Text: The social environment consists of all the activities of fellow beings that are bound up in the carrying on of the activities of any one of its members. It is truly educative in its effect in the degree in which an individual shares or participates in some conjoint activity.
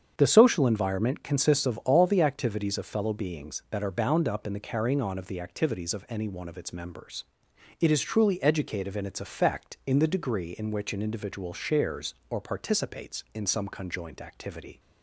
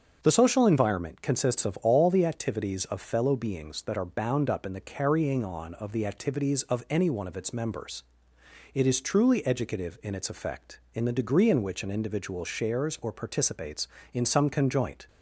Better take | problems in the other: first | starts louder than the rest; strong; until 1.2 s; 7 dB; strong in the first // stops before "activity"; at 15.0 s

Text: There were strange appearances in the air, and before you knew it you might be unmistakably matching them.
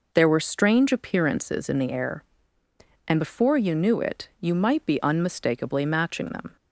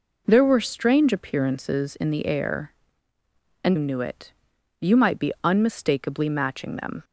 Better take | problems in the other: first | skips "before you"; at 3.7 s // pauses between "it" and "you"; noticeable; at 4.3 s; 0.48 s long

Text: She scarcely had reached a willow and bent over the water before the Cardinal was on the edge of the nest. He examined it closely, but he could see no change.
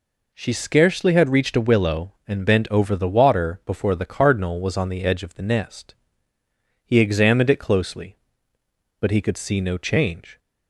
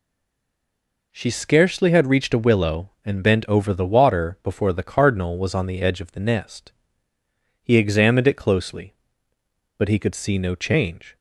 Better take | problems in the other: first | stays silent before the first word; until 1.1 s; 1.1 s long

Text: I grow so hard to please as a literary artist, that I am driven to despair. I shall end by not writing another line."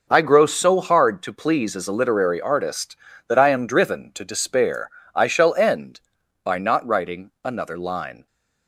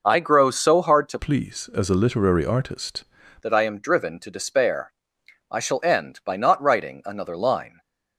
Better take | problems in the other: first | changes voice from "please" to "artist"; from 1.1 to 3.0 s; 1.9 s long

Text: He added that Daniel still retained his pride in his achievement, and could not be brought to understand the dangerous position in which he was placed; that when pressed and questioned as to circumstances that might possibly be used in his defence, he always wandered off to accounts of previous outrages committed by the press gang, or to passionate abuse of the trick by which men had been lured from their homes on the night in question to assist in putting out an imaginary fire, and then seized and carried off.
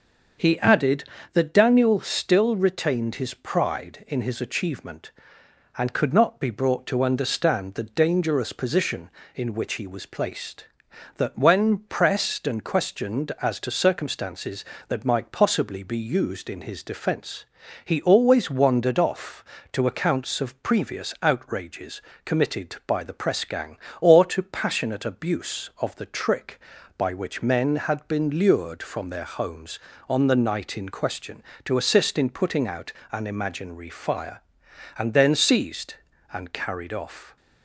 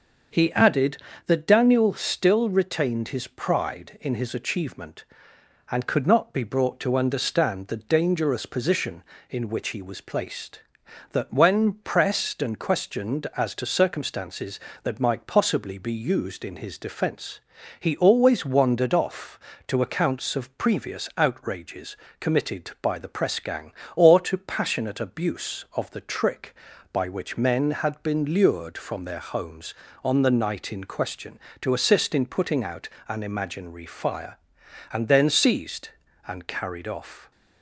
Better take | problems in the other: neither | starts louder than the rest; the same in both // pauses between "outrages" and "committed"; slight; the same in both // pauses between "out" and "an"; slight; the same in both

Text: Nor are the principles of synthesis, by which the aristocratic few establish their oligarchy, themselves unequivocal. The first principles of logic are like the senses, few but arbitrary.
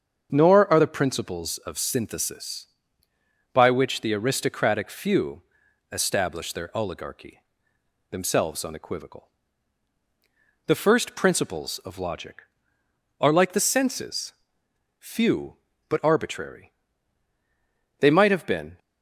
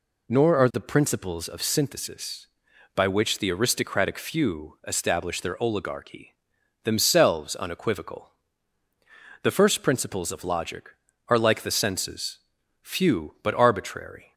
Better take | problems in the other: second | starts louder than the rest; strong; until 1.3 s; 7 dB // pauses between "few" and "establish"; noticeable; at 5.4 s; 0.50 s long // goes on to say "They might have been"; noticeable; from 17.9 s on; 0.80 s long

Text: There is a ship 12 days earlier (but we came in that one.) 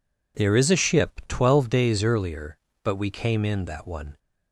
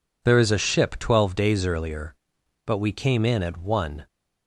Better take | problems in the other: first | says "at" for "that"; at 3.4 s

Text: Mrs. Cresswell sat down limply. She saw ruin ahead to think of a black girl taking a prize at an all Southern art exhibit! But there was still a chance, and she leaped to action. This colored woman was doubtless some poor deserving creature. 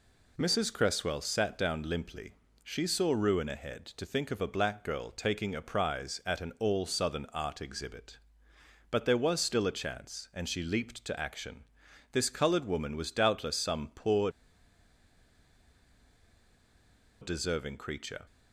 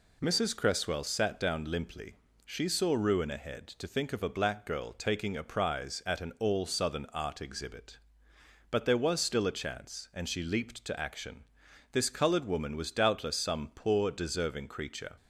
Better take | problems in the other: second | pauses between "poor" and "deserving"; strong; at 14.2 s; 2.9 s long

